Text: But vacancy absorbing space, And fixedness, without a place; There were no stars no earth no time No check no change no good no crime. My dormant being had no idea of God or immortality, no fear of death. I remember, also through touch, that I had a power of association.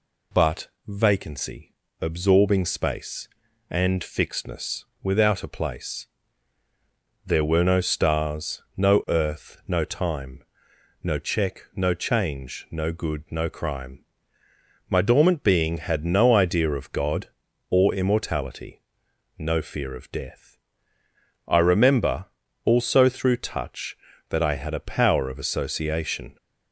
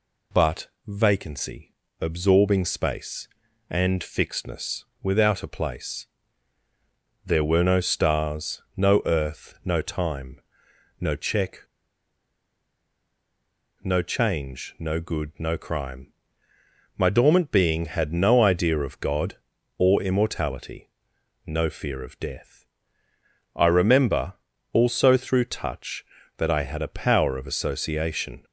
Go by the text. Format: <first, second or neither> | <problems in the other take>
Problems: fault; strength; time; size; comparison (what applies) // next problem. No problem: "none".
first | pauses between "But" and "vacancy"; slight; at 0.6 s; 0.18 s long; slight in the first // pauses between "vacancy" and "absorbing"; slight; at 1.7 s; 0.26 s long; slight in the first // pauses between "time" and "No"; noticeable; at 10.3 s; 0.62 s long; noticeable in the first // pauses between "check" and "no"; strong; at 11.6 s; 2.2 s long